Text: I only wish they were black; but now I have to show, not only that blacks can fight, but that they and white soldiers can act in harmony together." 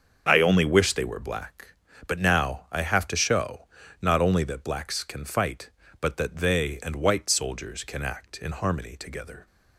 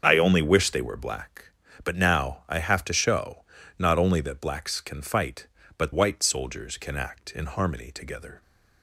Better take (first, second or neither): first